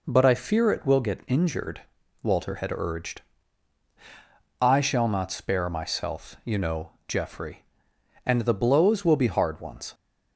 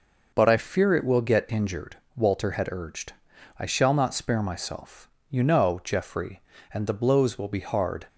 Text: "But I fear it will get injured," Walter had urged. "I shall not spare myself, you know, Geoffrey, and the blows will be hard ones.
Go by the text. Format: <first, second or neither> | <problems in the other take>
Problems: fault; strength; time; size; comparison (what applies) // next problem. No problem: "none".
first | stops before "ones"; at 8.0 s